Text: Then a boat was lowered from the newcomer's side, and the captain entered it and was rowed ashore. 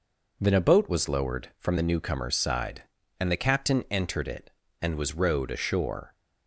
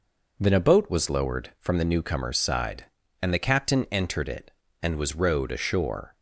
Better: neither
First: none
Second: none

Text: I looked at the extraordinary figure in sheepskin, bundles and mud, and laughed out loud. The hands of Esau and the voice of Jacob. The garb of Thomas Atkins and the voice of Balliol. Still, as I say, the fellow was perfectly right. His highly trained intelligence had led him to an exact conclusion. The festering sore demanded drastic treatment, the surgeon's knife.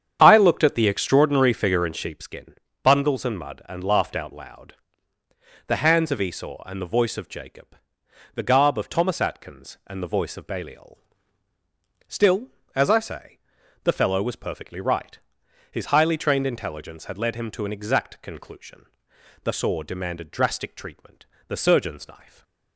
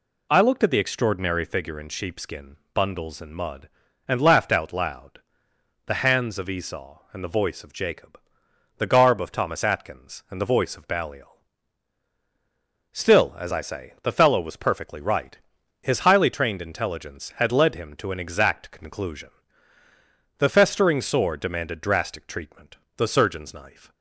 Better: second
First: starts louder than the rest; strong; until 1.2 s; 8 dB // skips "festering"; at 19.5 s // stays silent after the last word; slight; from 22.2 s on; 0.5 s long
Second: none

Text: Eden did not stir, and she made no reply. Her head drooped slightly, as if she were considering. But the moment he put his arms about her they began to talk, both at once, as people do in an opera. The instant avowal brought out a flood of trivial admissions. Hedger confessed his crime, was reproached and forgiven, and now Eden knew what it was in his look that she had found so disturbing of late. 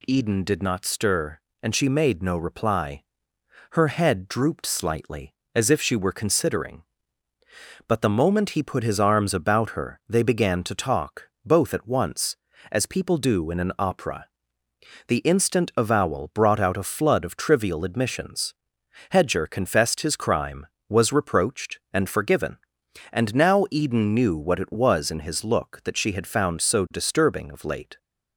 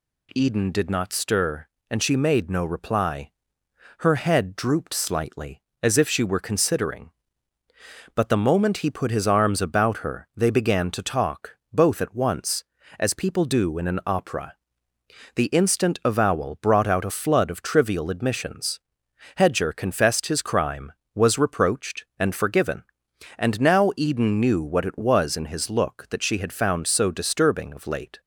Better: neither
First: none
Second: none

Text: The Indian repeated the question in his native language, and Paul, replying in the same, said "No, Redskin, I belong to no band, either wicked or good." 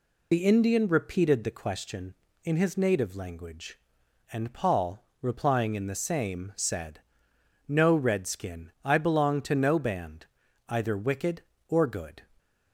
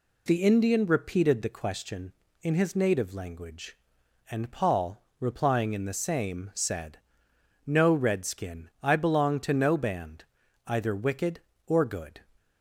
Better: second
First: loses the start of "The"; at 0.3 s; 40 ms // pauses between "said" and "No"; noticeable; at 7.0 s; 0.66 s long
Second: pauses between "said" and "No"; noticeable; at 6.9 s; 0.66 s long

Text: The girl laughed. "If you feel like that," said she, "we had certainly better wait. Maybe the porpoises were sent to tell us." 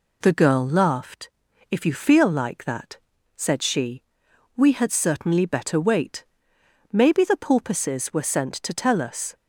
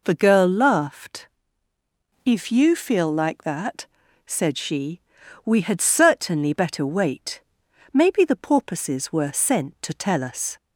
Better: neither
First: none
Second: none

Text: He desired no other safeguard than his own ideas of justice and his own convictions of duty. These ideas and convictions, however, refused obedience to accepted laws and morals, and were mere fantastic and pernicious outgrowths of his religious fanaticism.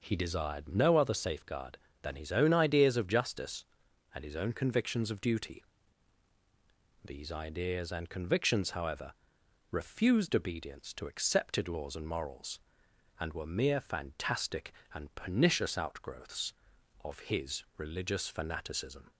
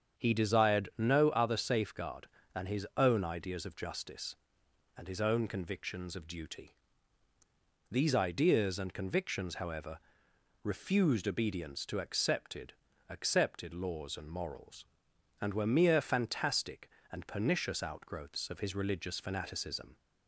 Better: first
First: none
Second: starts louder than the rest; strong; until 1.2 s; 7.5 dB // says "accepted" twice; at 13.0 s

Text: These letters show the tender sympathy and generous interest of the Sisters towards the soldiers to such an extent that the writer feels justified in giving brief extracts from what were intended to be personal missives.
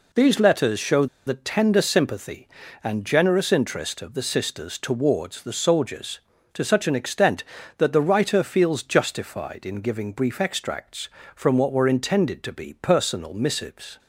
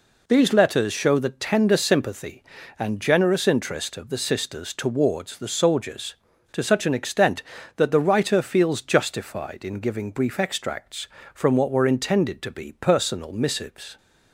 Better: second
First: pauses between "show" and "the"; slight; at 1.0 s; 0.20 s long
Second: none

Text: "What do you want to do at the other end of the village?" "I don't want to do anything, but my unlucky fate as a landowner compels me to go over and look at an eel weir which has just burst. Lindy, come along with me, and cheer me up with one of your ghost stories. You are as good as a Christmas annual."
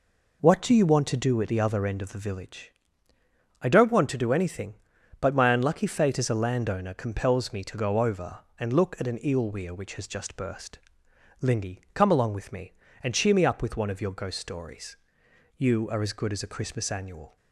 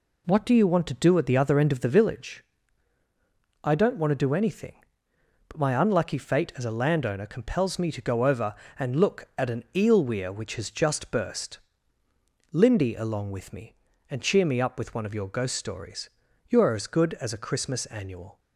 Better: first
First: none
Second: skips "come"; at 12.9 s

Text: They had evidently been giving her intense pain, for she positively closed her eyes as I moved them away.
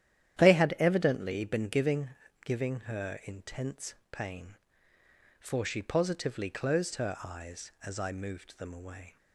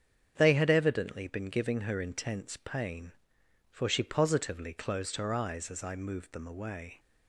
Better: second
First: starts louder than the rest; strong; until 1.4 s; 11 dB // says "giving" twice; at 2.4 s // pauses between "intense" and "pain"; slight; at 3.9 s; 0.16 s long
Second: starts louder than the rest; strong; until 1.3 s; 8 dB

